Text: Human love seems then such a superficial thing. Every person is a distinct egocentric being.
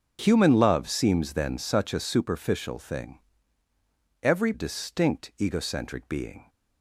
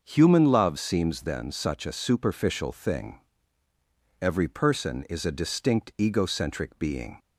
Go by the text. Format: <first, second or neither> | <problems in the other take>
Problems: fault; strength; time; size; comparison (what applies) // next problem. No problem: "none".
second | starts louder than the rest; until 1.2 s; 6.5 dB; also in the second // skips "person is a"; at 4.5 s